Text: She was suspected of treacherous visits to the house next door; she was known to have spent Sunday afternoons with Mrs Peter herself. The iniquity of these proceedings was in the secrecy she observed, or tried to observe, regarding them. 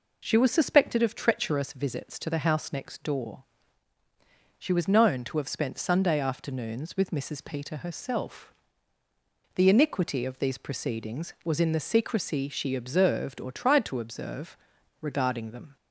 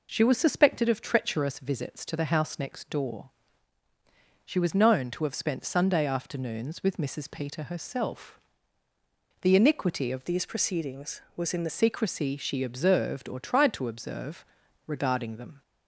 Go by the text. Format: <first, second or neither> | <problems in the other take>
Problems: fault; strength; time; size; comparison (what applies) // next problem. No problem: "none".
first | changes voice from "these" to "the"; from 10.2 to 11.7 s; 1.5 s long